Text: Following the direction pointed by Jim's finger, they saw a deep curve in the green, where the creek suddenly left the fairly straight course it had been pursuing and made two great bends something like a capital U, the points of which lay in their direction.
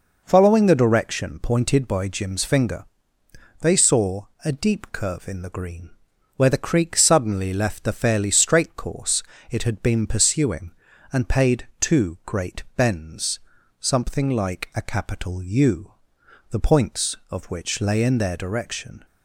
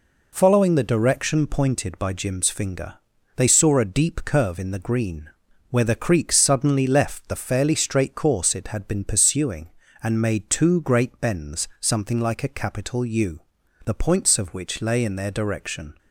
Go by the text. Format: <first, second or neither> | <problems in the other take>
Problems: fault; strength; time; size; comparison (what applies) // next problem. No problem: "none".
second | pauses between "saw" and "a"; slight; at 4.2 s; 0.20 s long // pauses between "course" and "it"; slight; at 9.2 s; 0.30 s long // says "paid" for "made"; at 11.2 s // pauses between "bends" and "something"; at 13.3 s; 0.40 s long